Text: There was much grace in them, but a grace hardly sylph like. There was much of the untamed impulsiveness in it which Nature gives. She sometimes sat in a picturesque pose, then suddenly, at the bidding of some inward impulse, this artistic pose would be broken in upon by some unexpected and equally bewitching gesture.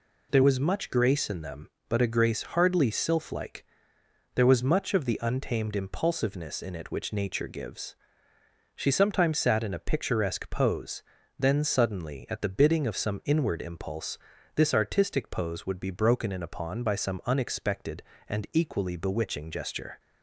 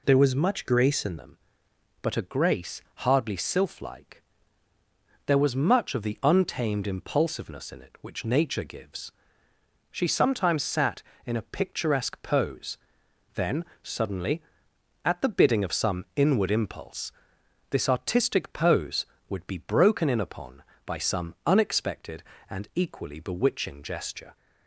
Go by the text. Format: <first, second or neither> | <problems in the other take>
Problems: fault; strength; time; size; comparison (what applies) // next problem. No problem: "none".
first | changes voice at "them"; from 1.1 s on; 23.2 s long // pauses between "then" and "suddenly"; slight; at 13.6 s; 0.20 s long